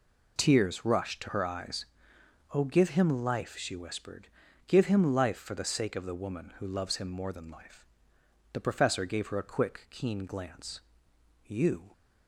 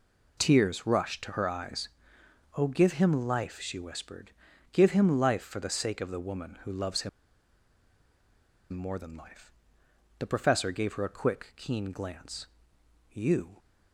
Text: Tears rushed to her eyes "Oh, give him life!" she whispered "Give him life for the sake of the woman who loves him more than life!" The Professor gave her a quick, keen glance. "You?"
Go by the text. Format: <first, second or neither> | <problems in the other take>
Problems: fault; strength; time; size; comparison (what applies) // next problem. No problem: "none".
first | pauses between "eyes" and "Oh"; noticeable; at 1.8 s; 0.68 s long; noticeable in the first // pauses between "whispered" and "Give"; at 4.3 s; 0.42 s long; also in the first // pauses between "him" and "more"; strong; at 7.0 s; 1.6 s long